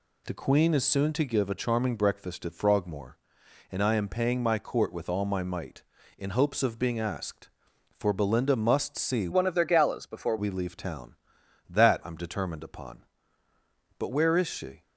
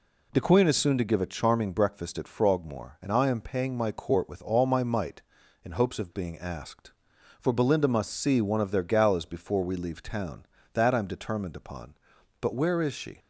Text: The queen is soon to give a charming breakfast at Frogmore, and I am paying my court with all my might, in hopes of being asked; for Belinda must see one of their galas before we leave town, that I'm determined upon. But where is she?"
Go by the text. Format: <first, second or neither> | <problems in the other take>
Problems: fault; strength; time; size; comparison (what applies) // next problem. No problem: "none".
second | changes voice from "one" to "before"; from 9.3 to 10.3 s; 1.0 s long